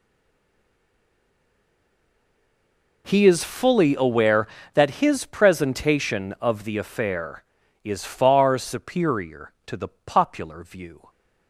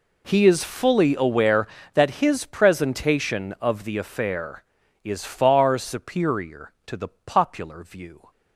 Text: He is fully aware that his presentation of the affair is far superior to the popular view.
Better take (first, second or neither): second